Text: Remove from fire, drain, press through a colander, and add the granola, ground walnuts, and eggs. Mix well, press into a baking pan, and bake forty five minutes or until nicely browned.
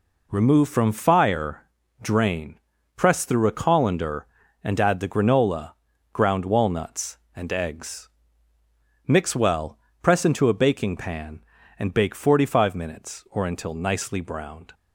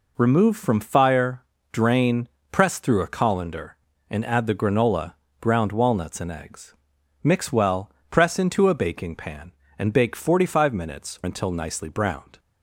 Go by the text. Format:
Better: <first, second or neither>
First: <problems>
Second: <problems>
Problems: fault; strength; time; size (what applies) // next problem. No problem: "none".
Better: first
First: none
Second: skips "or"; at 11.2 s